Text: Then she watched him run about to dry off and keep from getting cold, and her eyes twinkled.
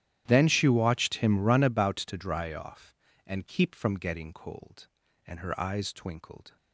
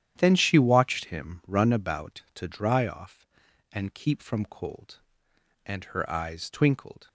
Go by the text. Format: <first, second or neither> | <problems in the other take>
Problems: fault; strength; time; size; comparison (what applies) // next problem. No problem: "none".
first | starts louder than the rest; strong; until 1.1 s; 10 dB; strong in the first // skips "getting"; at 4.4 s